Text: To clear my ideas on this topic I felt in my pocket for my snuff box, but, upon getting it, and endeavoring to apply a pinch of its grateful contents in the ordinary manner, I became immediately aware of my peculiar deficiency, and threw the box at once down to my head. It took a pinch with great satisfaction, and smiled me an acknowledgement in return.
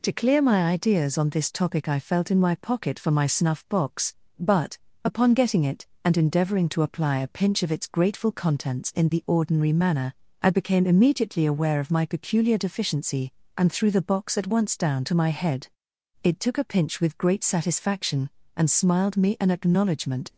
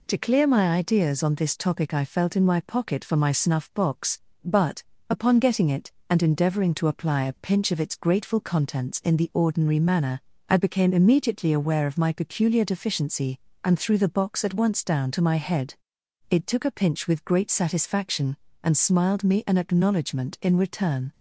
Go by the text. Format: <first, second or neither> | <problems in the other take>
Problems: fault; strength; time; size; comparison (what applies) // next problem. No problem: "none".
second | stops before "in return"; at 20.3 s